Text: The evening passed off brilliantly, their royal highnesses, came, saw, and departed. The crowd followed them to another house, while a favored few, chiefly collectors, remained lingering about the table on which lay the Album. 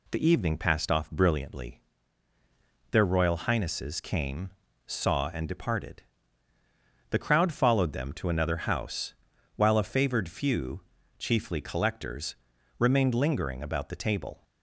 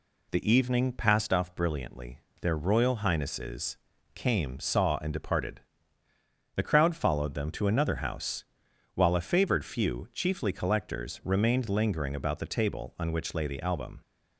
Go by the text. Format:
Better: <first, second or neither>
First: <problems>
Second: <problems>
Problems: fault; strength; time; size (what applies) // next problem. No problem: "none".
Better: second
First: stops before "on which lay the Album"; at 14.4 s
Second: none